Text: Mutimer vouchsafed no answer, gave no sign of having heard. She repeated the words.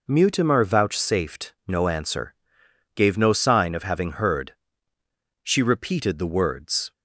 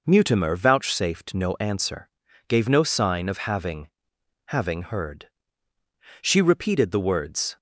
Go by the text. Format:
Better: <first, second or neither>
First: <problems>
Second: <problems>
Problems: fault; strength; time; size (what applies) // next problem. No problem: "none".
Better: first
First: none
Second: says "having" twice; at 4.4 s